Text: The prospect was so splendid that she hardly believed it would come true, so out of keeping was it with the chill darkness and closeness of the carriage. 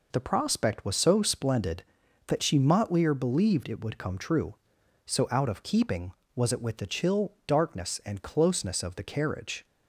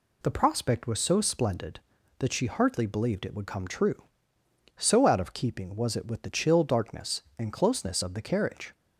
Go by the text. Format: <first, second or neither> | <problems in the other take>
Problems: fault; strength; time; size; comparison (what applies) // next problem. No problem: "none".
second | says "motlier" for "hardly"; at 2.5 s